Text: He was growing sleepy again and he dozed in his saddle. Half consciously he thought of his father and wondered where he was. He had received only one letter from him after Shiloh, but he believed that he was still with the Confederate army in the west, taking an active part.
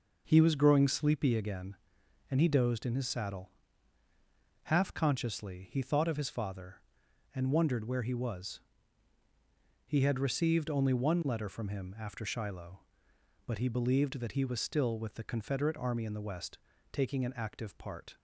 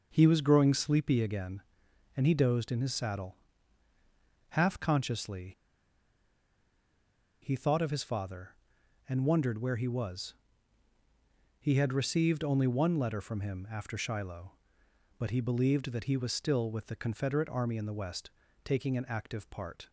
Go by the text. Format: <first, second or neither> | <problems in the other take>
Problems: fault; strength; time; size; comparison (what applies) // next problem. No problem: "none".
first | pauses between "consciously" and "he"; strong; at 5.5 s; 1.8 s long